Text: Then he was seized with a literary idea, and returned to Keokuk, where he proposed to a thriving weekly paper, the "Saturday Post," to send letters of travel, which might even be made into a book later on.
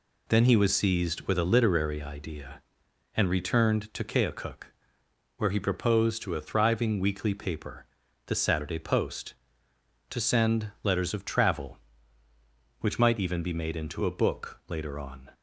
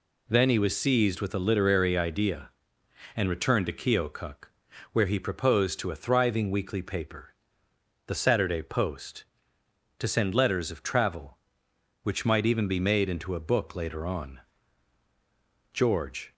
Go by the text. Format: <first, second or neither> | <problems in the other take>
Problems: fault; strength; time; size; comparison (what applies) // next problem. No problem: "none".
first | goes on to say "George"; from 15.7 s on; 0.60 s long